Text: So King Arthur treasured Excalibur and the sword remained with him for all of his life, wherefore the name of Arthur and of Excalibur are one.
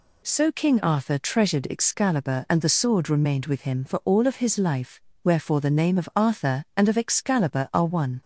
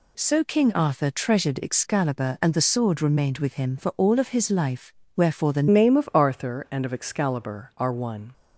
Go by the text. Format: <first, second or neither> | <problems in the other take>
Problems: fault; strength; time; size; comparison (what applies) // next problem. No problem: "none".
first | changes voice at "name"; from 5.6 s on; 2.7 s long